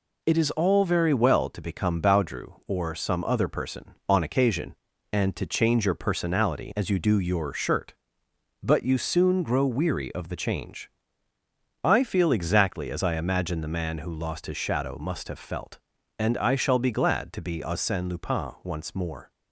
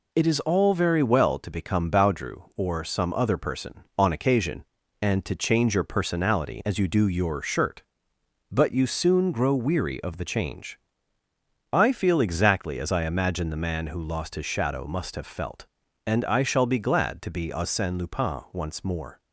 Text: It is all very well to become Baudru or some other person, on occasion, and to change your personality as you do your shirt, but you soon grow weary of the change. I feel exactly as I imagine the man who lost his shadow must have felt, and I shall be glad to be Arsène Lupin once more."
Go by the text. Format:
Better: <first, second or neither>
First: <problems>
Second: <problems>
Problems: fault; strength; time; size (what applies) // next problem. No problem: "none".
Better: neither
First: none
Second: none